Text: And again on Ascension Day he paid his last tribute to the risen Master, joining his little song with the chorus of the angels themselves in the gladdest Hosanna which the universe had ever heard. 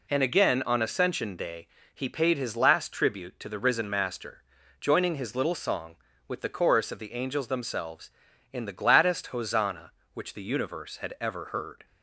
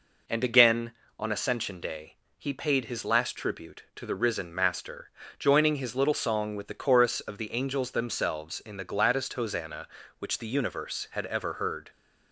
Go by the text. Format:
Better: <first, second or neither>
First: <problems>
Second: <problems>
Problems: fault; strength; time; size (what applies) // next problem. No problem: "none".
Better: neither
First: pauses between "Day" and "he"; slight; at 1.6 s; 0.26 s long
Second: pauses between "Day" and "he"; slight; at 2.1 s; 0.24 s long